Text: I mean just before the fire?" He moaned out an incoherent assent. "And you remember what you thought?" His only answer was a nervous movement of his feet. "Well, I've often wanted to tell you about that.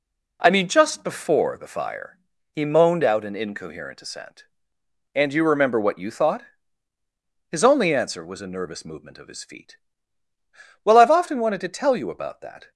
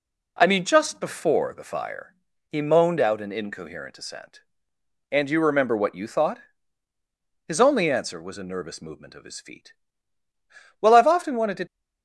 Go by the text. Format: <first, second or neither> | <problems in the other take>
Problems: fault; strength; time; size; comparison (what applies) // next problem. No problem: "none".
first | stops before "tell you about that"; at 11.6 s